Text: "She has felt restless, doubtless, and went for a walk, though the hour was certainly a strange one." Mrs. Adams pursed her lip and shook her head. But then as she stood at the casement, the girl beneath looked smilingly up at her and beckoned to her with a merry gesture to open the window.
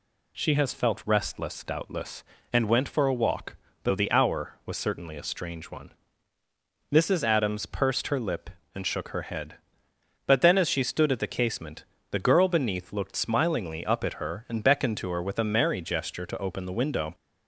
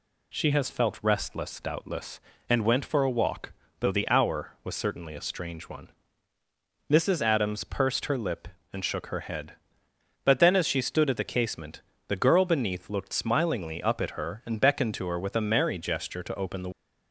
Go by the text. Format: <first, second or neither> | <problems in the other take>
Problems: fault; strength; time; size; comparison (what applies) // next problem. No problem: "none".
first | stops before "window"; at 16.7 s